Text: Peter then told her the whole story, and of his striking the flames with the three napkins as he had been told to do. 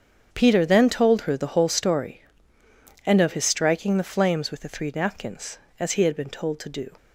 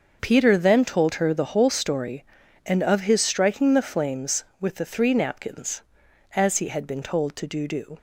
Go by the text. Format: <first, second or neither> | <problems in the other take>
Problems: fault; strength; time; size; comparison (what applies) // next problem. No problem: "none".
first | starts louder than the rest; noticeable; until 1.2 s; 6 dB; strong in the first // says "do" twice; at 7.6 s